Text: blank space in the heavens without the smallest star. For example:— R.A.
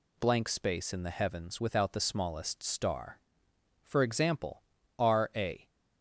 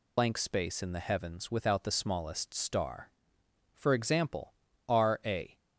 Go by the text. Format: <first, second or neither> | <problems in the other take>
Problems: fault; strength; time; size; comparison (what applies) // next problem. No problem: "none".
first | loses the start of "blank"; at 0.1 s; 95 ms